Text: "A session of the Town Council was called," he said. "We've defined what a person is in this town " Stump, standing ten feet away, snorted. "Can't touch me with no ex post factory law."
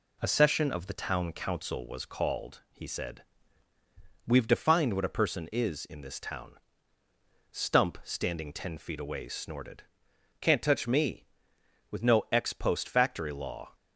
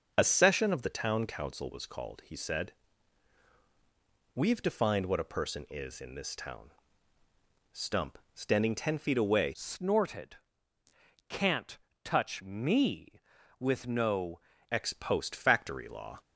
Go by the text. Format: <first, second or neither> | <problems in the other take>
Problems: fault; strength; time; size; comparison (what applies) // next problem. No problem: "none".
first | starts louder than the rest; until 1.1 s; 7 dB // changes voice from "snorted" to "no"; from 9.5 to 14.3 s; 4.8 s long // pauses between "Can't" and "touch"; slight; at 11.7 s; 0.26 s long